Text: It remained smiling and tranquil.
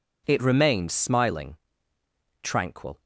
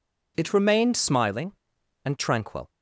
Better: second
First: skips "and"; at 2.0 s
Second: none

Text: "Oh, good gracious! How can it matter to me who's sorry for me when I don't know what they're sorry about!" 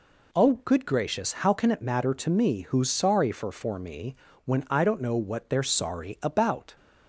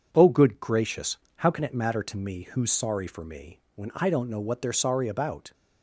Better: second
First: says "for" twice; at 3.5 s // pauses between "me" and "when"; slight; at 4.1 s; 0.30 s long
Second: none

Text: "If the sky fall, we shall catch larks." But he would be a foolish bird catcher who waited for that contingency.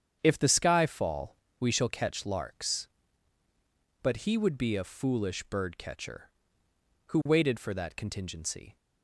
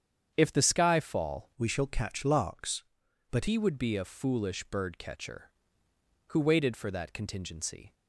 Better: first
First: starts louder than the rest; strong; until 1.2 s; 8 dB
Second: starts louder than the rest; strong; until 1.3 s; 8 dB // changes voice from "we" to "But"; from 1.5 to 3.4 s; 1.9 s long

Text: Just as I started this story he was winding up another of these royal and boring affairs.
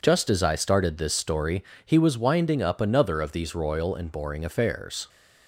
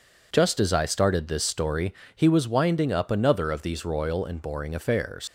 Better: first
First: pauses between "story" and "he"; slight; at 1.6 s; 0.22 s long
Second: pauses between "story" and "he"; slight; at 1.9 s; 0.22 s long // leaves "affairs" unfinished; at 5.2 s; 110 ms

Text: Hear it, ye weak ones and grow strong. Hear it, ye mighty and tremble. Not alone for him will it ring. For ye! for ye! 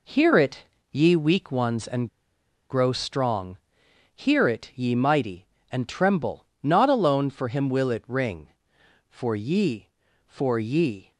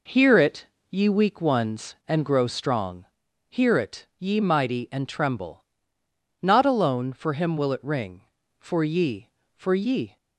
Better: second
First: pauses between "and" and "grow"; noticeable; at 2.0 s; 0.62 s long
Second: none

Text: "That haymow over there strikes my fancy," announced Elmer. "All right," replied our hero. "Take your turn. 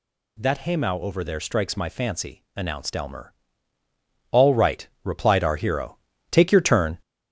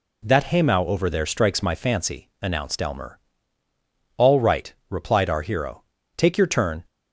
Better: second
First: gets louder; throughout; 4 dB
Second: none

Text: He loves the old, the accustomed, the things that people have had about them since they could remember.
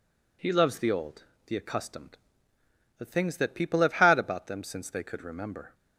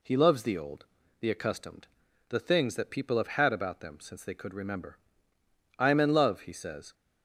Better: first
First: none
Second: goes on to say "I am in love he says"; noticeable; from 5.7 s on; 1.1 s long

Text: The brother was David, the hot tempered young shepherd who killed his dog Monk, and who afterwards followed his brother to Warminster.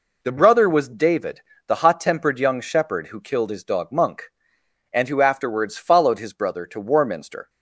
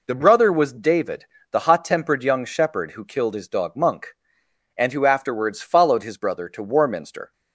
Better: neither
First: none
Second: none

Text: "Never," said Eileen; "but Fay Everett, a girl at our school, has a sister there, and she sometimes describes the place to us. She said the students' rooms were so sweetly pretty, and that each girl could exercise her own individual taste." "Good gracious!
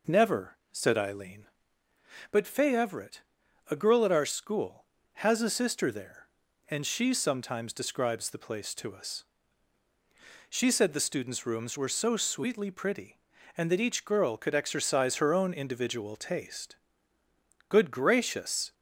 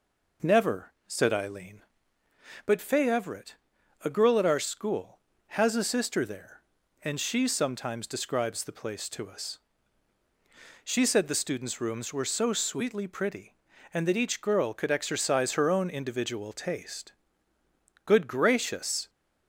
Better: neither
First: none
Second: none

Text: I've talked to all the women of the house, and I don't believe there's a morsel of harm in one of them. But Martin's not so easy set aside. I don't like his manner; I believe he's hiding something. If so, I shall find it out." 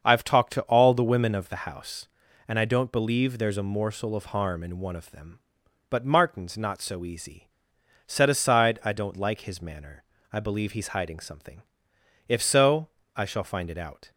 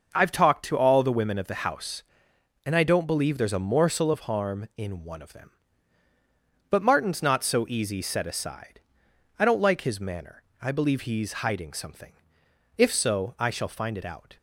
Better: second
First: starts louder than the rest; until 1.0 s; 6.5 dB // pauses between "easy" and "set"; noticeable; at 7.4 s; 0.58 s long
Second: none

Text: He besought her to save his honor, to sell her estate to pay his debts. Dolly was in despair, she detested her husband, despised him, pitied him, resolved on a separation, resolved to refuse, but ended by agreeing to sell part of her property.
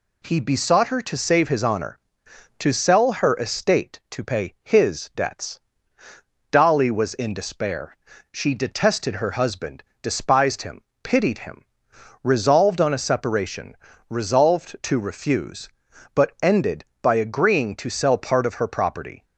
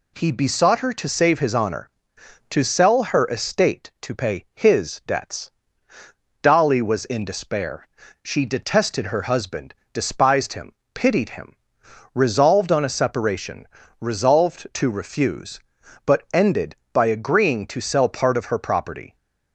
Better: neither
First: none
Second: none

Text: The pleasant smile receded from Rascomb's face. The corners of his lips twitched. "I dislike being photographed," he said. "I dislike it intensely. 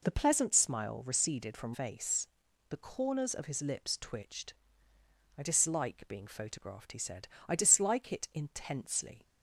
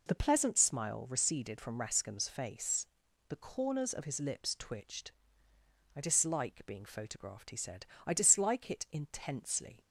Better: second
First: skips "Rascomb's"; at 1.7 s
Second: none

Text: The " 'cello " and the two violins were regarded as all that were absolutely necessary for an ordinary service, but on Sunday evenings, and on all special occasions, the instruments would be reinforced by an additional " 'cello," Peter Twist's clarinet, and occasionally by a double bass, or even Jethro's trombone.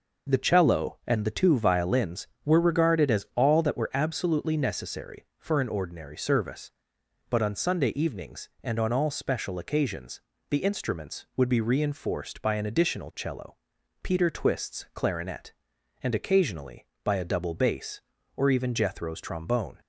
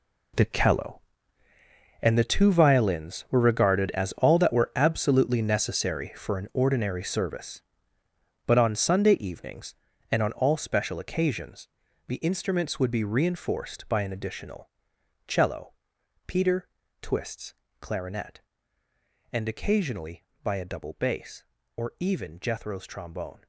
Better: first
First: none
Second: gets quieter; strong; throughout; 10.5 dB // pauses between "Peter" and "Twist's"; slight; at 16.6 s; 0.34 s long // pauses between "Twist's" and "clarinet"; slight; at 17.5 s; 0.24 s long

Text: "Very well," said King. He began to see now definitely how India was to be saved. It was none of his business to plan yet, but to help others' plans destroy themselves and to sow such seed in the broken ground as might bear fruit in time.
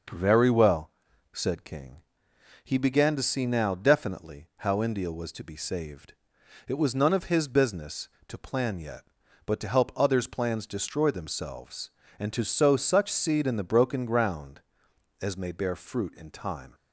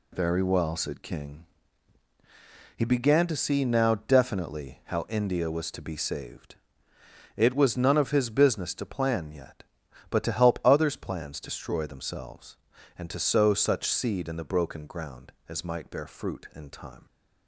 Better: second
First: says "may" for "might"; at 15.3 s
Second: none

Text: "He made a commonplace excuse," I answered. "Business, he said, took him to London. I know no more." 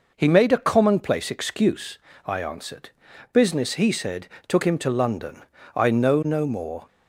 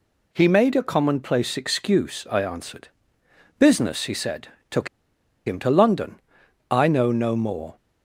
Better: first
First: none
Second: pauses between "took" and "him"; noticeable; at 4.8 s; 0.59 s long

